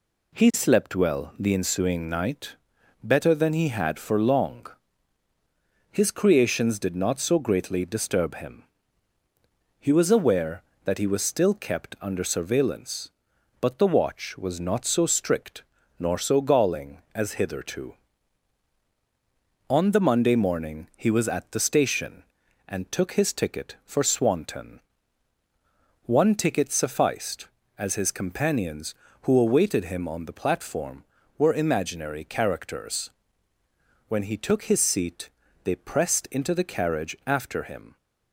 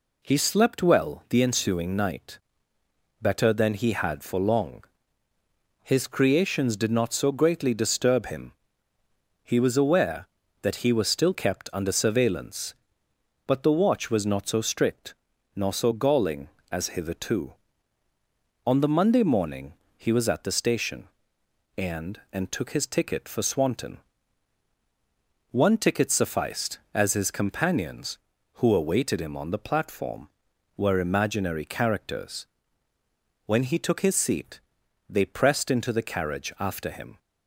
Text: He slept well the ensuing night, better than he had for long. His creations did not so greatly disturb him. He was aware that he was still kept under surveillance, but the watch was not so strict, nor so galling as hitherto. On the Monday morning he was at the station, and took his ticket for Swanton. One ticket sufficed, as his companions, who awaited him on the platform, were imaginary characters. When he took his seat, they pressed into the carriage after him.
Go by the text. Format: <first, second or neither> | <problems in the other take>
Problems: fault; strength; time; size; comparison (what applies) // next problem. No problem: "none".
first | pauses between "morning" and "he"; slight; at 19.7 s; 0.22 s long // says "and" twice; at 22.3 s